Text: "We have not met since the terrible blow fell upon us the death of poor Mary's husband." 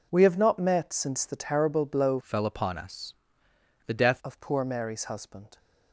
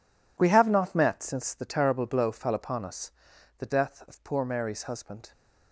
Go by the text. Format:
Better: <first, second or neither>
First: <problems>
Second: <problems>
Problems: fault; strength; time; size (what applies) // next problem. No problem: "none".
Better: second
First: changes voice from "fell" to "death"; from 2.2 to 4.2 s; 2.0 s long // pauses between "us" and "the"; noticeable; at 3.1 s; 0.72 s long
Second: pauses between "us" and "the"; noticeable; at 3.1 s; 0.46 s long